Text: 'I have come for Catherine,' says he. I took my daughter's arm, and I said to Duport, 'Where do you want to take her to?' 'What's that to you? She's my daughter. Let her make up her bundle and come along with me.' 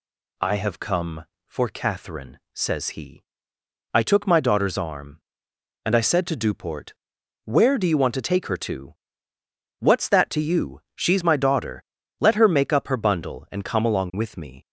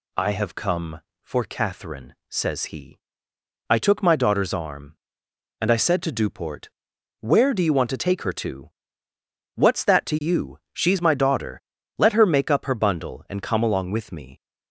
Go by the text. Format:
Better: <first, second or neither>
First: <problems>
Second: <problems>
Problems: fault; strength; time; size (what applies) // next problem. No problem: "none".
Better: neither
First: none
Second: none